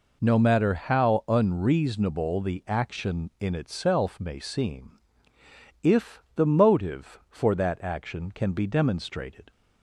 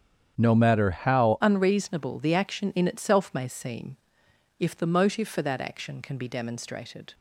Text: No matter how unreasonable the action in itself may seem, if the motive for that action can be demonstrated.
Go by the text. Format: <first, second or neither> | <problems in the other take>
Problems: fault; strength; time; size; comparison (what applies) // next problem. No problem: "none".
first | starts louder than the rest; strong; until 1.3 s; 8.5 dB // changes voice at "unreasonable"; from 1.4 s on; 5.7 s long